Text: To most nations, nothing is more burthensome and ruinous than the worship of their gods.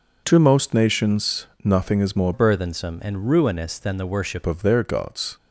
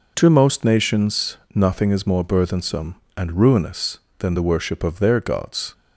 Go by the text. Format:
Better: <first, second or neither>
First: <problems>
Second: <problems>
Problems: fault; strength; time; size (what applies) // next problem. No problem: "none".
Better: second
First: changes voice from "burthensome" to "worship"; from 2.3 to 4.4 s; 2.1 s long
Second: none